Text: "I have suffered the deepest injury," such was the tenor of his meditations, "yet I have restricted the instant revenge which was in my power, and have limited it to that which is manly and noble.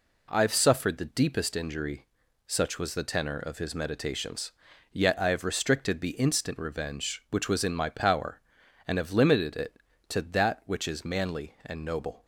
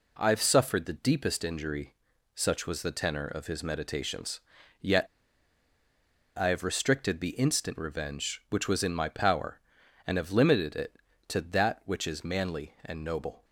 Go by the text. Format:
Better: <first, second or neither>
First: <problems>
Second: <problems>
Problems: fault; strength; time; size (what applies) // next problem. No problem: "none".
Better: first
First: none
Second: pauses between "yet" and "I"; strong; at 5.0 s; 1.2 s long